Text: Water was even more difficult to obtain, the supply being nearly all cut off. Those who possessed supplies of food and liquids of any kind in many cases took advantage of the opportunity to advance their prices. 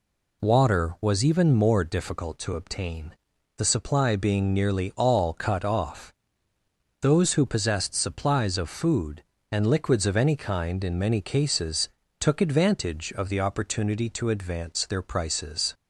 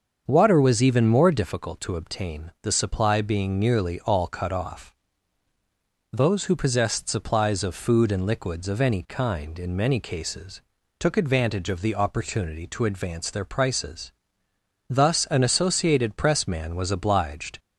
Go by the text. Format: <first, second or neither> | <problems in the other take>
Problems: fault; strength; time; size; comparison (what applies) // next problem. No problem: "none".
first | starts louder than the rest; until 1.2 s; 7 dB // pauses between "cases" and "took"; at 10.6 s; 0.38 s long; slight in the first // goes on to say "Thus an Associated Press man was obliged"; strong; from 14.8 s on; 2.7 s long